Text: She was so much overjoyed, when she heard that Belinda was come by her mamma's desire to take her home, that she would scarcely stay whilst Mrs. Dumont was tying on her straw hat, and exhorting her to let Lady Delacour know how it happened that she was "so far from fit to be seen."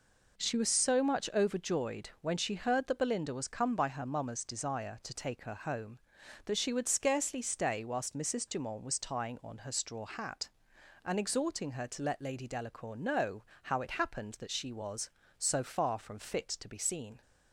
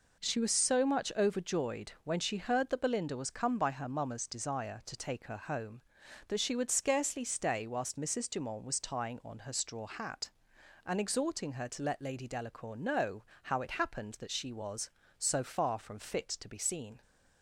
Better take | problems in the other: neither | pauses between "know" and "how"; slight; the same in both

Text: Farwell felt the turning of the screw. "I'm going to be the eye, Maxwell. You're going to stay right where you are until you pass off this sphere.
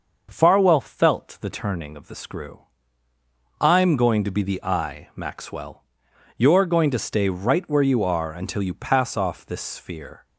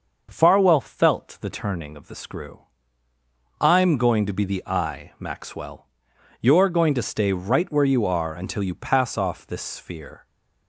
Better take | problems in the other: neither | starts louder than the rest; noticeable; the same in both

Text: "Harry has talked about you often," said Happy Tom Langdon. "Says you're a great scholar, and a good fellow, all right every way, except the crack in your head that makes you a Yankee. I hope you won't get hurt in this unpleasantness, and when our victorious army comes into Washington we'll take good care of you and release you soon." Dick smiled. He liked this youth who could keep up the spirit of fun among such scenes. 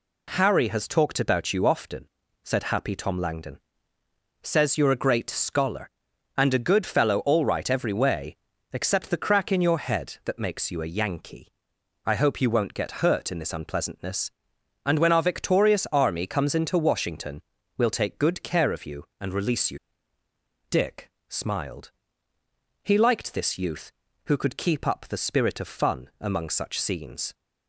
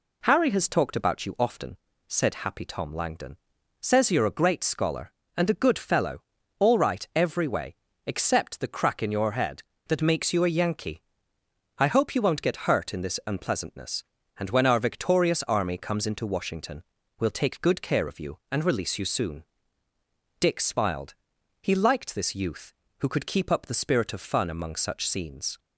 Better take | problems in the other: second | pauses between "Washington" and "we'll"; at 17.4 s; 0.38 s long; slight in the second // skips "soon"; at 20.2 s // pauses between "Dick" and "smiled"; slight; at 21.0 s; 0.20 s long

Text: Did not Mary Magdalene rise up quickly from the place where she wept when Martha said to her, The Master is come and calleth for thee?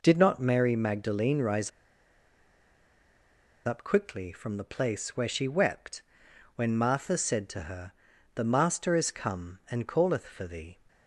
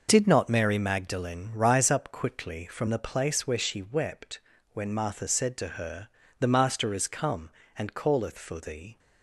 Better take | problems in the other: second | pauses between "rise" and "up"; strong; at 1.7 s; 1.9 s long // pauses between "wept" and "when"; noticeable; at 6.0 s; 0.54 s long; slight in the second

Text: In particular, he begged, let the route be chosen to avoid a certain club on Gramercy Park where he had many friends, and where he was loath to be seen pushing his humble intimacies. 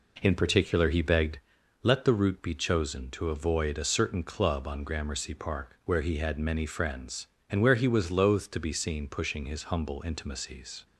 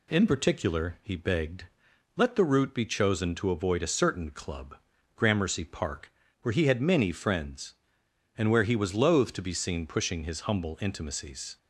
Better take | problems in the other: first | skips "on"; at 4.9 s // pauses between "Park" and "where"; slight; at 6.1 s; 0.30 s long

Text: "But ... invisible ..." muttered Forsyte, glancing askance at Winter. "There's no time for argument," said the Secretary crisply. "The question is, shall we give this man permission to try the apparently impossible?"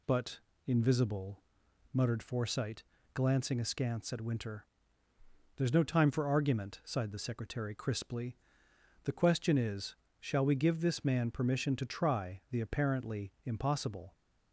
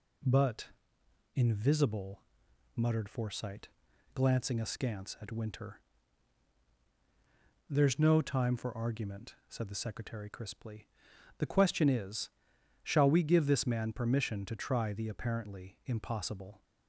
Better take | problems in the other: second | says "sighed" for "said"; at 6.8 s

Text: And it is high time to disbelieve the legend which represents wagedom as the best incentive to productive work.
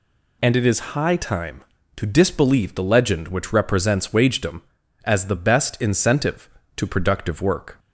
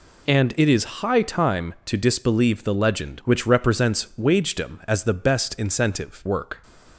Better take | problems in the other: first | skips "to productive"; at 6.2 s

